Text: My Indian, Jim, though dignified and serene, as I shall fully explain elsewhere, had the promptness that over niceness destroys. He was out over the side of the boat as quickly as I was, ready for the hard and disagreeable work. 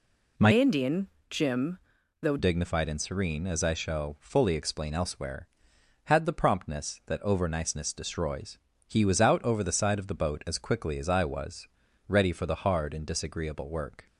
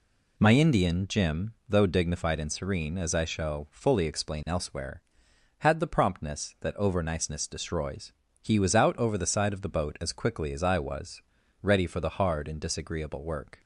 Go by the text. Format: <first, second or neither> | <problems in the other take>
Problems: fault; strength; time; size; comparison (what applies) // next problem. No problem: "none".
second | changes voice from "Indian" to "though"; from 0.5 to 2.3 s; 1.8 s long